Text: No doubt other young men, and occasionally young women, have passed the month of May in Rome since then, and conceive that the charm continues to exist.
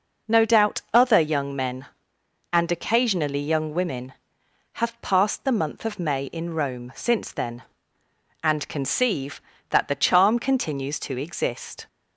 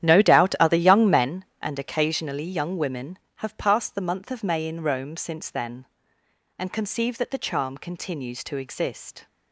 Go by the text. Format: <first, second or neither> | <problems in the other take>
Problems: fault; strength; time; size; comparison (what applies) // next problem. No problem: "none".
first | starts louder than the rest; strong; until 1.3 s; 11 dB